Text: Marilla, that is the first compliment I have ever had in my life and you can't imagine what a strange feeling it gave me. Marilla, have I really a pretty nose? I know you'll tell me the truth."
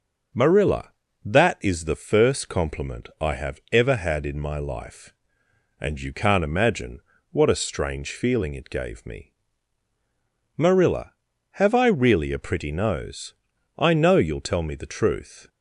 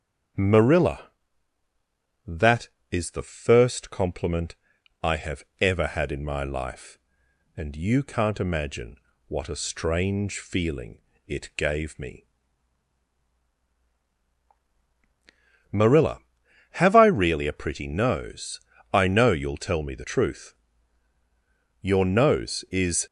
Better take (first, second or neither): first